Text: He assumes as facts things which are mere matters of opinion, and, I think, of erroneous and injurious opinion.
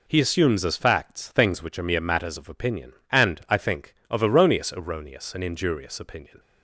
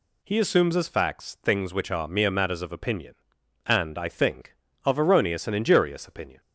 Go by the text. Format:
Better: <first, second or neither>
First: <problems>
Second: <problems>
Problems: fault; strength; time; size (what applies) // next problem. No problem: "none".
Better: second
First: says "erroneous" twice; at 4.7 s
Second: none